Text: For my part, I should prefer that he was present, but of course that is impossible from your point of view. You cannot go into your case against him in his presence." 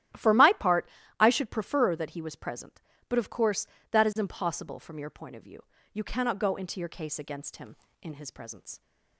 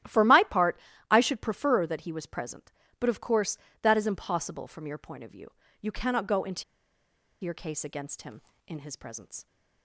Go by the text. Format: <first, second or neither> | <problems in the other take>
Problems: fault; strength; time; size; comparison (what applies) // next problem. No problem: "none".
first | starts louder than the rest; strong; until 1.3 s; 12 dB; strong in the first // pauses between "into" and "your"; noticeable; at 6.6 s; 0.80 s long